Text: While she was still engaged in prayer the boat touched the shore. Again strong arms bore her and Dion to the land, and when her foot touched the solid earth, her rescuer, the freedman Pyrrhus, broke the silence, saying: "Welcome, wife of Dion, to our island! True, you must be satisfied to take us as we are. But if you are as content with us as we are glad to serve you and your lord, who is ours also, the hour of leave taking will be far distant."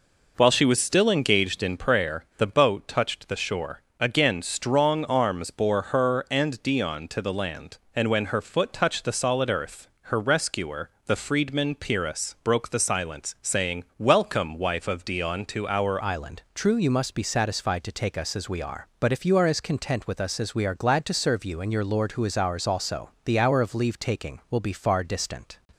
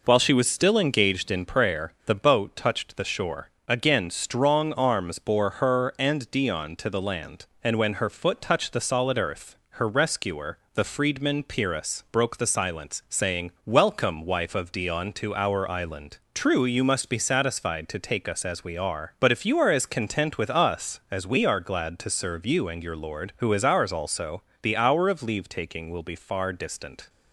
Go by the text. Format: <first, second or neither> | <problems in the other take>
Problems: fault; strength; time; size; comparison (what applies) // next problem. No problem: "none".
second | changes voice at "island"; from 16.0 s on; 9.5 s long